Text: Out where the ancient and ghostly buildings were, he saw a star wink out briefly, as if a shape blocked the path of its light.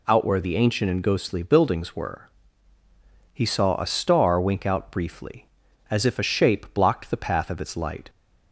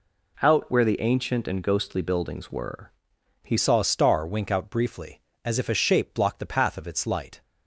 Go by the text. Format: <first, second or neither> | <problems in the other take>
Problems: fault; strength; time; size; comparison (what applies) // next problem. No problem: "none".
first | changes voice at "saw"; from 3.5 s on; 3.9 s long